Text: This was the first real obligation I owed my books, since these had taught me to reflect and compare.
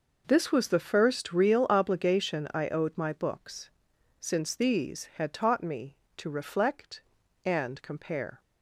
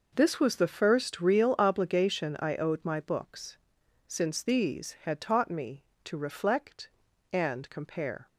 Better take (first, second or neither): neither